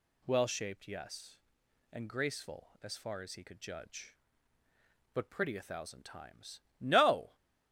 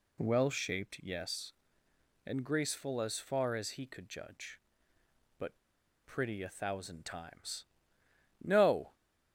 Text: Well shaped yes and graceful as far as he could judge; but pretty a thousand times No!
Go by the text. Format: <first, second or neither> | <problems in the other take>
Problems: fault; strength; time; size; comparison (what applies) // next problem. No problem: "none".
first | pauses between "but" and "pretty"; noticeable; at 5.5 s; 0.47 s long // pauses between "times" and "No"; noticeable; at 7.6 s; 0.76 s long; slight in the first